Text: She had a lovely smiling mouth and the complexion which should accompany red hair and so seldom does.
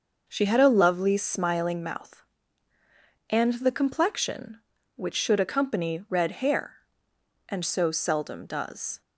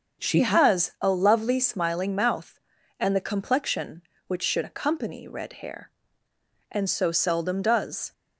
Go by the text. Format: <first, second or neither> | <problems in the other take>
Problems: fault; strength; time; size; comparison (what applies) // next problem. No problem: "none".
first | starts louder than the rest; until 1.2 s; 6 dB // says "has" for "had"; at 0.4 s